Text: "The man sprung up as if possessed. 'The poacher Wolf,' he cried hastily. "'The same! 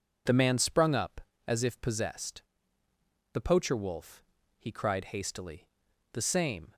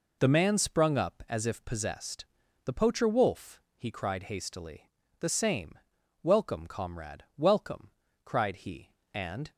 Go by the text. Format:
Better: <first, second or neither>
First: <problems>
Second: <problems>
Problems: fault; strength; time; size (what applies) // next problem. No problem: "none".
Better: first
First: none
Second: goes on to say "Welcome comrade welcome cried he and"; strong; from 6.2 s on; 3.2 s long